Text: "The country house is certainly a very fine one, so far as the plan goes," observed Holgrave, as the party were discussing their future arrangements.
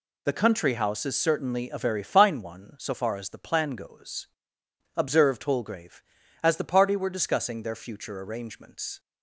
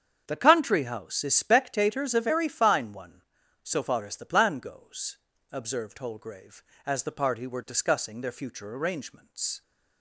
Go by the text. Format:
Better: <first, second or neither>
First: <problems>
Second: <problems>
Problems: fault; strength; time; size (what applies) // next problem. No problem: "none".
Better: first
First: none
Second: starts louder than the rest; strong; until 1.2 s; 8 dB // says "spectators" for "certainly"; at 1.3 s